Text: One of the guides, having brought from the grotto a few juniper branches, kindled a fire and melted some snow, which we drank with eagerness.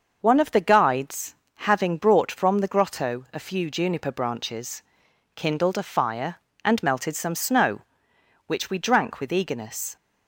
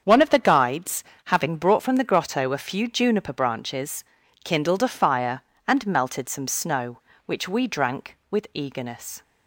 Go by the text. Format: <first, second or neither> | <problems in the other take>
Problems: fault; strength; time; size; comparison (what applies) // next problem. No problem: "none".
neither | starts louder than the rest; the same in both